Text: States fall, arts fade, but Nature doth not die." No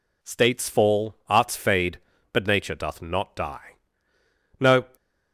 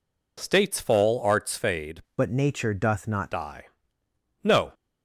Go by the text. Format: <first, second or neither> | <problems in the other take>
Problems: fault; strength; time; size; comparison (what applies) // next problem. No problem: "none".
first | changes voice from "but" to "not"; from 2.1 to 3.3 s; 1.2 s long